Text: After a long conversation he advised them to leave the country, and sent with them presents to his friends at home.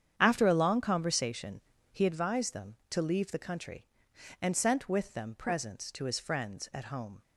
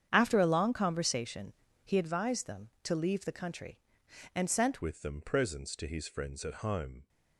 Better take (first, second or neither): first